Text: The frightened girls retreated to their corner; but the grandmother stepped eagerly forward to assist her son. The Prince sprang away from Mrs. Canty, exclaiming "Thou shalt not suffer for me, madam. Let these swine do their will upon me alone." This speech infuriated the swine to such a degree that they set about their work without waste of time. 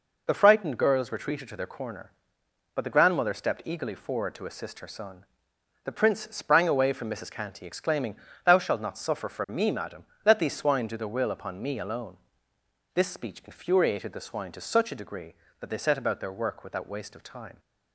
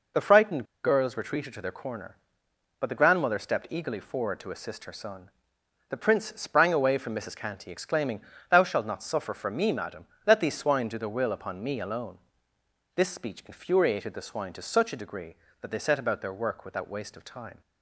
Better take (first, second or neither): first